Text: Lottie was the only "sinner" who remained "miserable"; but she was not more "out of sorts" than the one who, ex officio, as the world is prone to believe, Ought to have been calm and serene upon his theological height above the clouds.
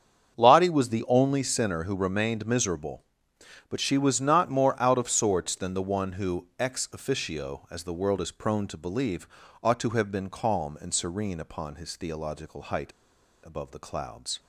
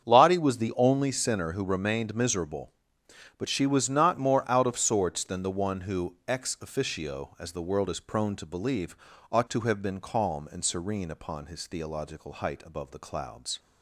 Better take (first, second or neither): second